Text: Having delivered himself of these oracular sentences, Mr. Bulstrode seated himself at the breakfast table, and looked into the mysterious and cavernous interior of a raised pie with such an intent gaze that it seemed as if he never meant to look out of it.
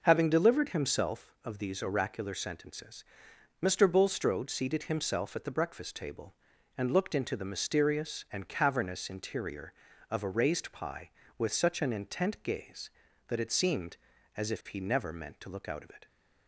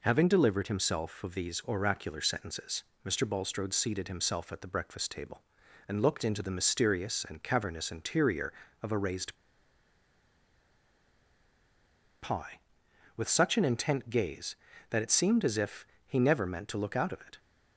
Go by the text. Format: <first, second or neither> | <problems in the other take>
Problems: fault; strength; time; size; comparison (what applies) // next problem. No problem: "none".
first | pauses between "raised" and "pie"; strong; at 9.3 s; 2.8 s long // pauses between "if" and "he"; slight; at 15.8 s; 0.20 s long